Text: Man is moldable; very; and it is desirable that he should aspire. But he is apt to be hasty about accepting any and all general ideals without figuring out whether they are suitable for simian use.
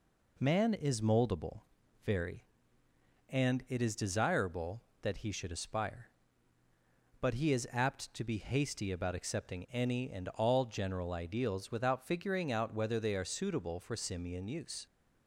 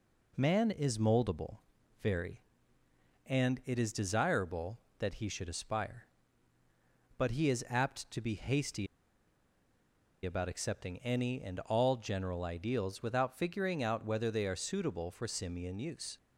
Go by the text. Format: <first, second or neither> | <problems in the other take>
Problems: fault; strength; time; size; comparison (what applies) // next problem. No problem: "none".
first | pauses between "hasty" and "about"; strong; at 8.8 s; 1.3 s long